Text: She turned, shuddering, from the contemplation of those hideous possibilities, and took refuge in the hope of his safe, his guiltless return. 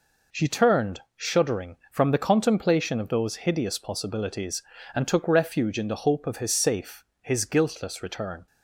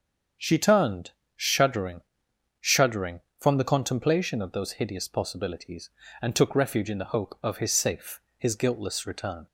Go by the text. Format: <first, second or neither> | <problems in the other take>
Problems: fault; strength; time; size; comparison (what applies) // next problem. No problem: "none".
first | starts louder than the rest; strong; until 1.6 s; 7.5 dB // says "shuddering" twice; at 2.6 s